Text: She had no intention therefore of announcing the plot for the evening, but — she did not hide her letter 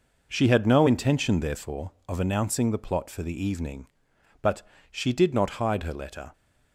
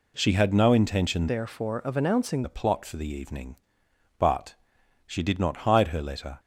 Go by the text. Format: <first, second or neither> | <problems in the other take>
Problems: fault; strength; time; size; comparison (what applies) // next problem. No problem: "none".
first | changes voice from "therefore" to "announcing"; from 1.2 to 2.4 s; 1.2 s long